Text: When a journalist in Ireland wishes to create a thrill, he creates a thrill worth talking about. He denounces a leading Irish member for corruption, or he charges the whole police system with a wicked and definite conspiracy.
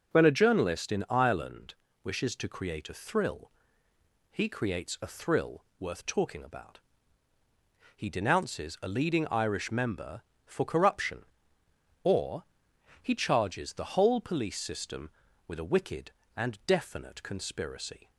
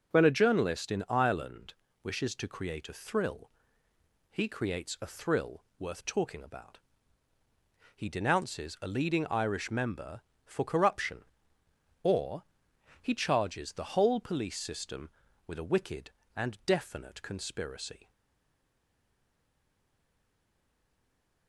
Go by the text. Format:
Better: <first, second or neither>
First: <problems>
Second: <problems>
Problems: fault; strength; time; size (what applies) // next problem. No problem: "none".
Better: first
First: pauses between "Ireland" and "wishes"; slight; at 1.7 s; 0.32 s long // pauses between "thrill" and "worth"; slight; at 5.6 s; 0.16 s long // pauses between "or" and "he"; noticeable; at 12.4 s; 0.58 s long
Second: pauses between "Ireland" and "wishes"; slight; at 1.7 s; 0.32 s long // pauses between "thrill" and "worth"; slight; at 5.6 s; 0.16 s long // pauses between "or" and "he"; noticeable; at 12.4 s; 0.58 s long // stays silent after the last word; strong; from 18.0 s on; 3.4 s long